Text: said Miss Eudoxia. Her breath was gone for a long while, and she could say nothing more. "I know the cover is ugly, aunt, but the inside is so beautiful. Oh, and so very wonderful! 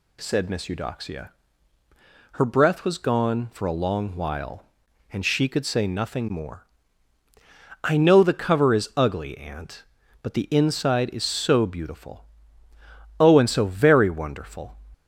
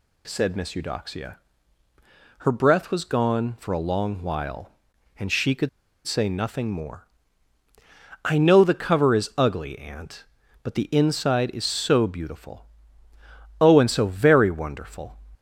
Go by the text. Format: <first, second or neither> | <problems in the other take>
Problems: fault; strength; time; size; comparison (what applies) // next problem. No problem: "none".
first | pauses between "could" and "say"; at 5.6 s; 0.37 s long